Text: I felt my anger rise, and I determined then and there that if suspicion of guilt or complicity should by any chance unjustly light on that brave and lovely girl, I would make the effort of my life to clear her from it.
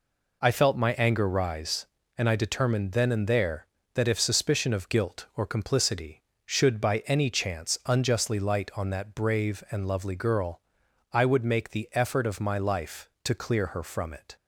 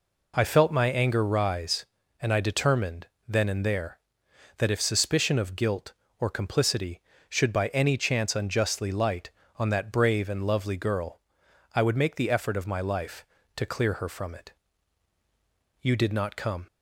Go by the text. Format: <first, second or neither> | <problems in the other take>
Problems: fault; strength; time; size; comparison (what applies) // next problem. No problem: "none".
first | pauses between "determined" and "then"; slight; at 3.0 s; 0.22 s long // goes on to say "You did not come"; noticeable; from 15.8 s on; 0.86 s long